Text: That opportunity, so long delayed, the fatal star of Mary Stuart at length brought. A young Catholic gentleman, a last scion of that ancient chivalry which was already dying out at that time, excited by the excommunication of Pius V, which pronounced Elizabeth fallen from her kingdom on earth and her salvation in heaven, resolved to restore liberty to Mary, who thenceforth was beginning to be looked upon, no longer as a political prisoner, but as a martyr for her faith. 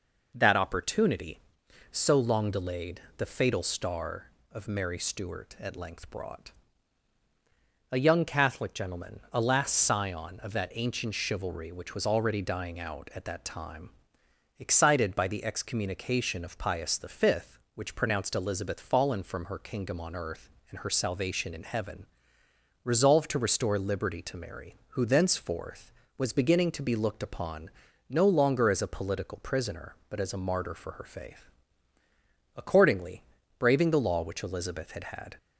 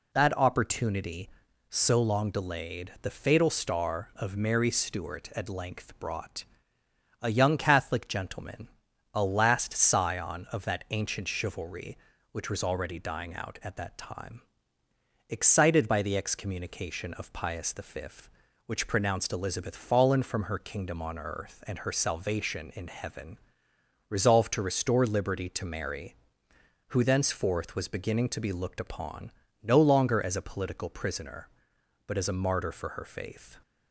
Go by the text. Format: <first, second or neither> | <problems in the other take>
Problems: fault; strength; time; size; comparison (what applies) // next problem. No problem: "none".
second | goes on to say "Accordingly braving the law which Elizabeth had had"; strong; from 32.5 s on; 2.8 s long